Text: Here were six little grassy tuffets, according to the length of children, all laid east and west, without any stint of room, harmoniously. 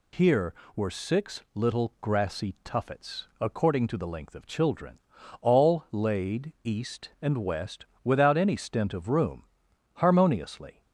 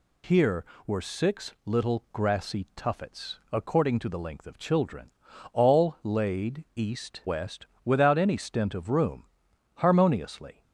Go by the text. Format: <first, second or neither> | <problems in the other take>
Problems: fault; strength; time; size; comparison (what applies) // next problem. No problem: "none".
first | skips "and"; at 7.2 s